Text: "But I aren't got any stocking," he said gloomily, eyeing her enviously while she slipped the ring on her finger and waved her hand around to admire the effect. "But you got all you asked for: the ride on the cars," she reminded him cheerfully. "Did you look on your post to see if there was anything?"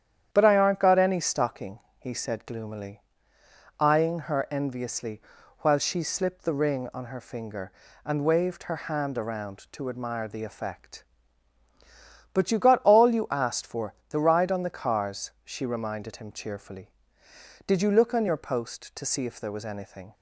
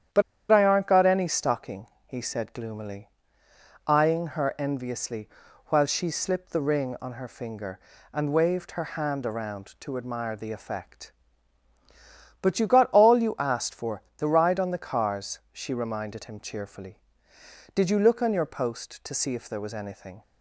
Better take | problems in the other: first | starts louder than the rest; strong; until 1.4 s; 9 dB; strong in the first // pauses between "But" and "I"; slight; at 0.2 s; 0.30 s long // pauses between "enviously" and "while"; at 5.3 s; 0.38 s long; also in the first

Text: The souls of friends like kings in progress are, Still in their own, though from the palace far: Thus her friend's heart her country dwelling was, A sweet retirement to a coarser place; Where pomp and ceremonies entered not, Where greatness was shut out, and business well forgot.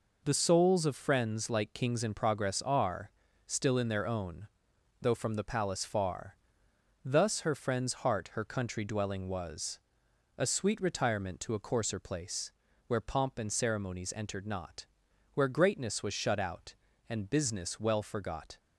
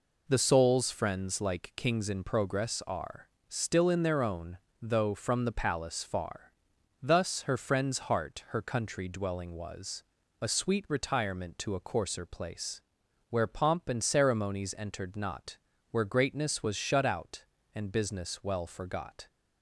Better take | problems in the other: first | skips "of"; at 0.9 s

